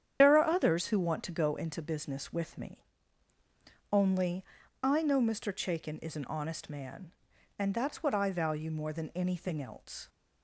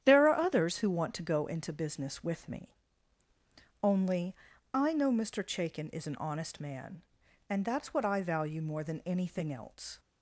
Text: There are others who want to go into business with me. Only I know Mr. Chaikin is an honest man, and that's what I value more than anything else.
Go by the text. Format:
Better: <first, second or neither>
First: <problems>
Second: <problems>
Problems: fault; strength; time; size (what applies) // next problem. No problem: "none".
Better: second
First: loses the start of "There"; at 0.2 s; 75 ms // starts louder than the rest; strong; until 1.2 s; 9 dB // pauses between "Only" and "I"; at 4.4 s; 0.40 s long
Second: starts louder than the rest; strong; until 1.0 s; 10 dB // pauses between "Only" and "I"; at 4.3 s; 0.40 s long